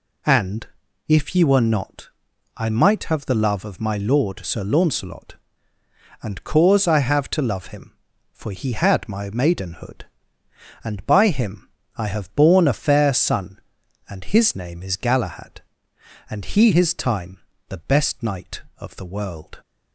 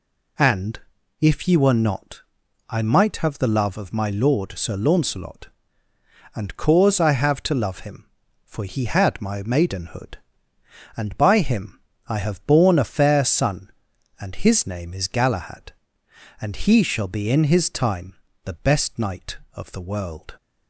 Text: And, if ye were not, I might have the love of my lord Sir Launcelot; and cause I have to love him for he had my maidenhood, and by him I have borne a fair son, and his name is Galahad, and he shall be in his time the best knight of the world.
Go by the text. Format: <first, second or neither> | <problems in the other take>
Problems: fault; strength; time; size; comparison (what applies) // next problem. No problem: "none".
second | pauses between "him" and "I"; slight; at 11.6 s; 0.26 s long; slight in the second // skips "shall be in"; at 16.7 s // pauses between "time" and "the"; slight; at 17.3 s; 0.30 s long; slight in the second